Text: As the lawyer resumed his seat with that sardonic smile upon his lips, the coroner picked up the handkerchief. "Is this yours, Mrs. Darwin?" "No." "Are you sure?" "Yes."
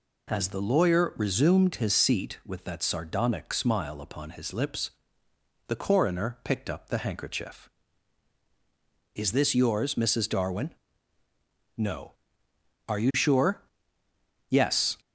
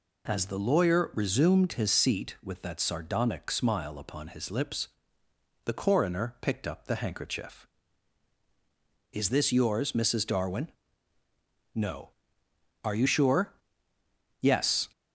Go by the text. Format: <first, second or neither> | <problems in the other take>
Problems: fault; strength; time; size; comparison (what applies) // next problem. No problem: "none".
neither | none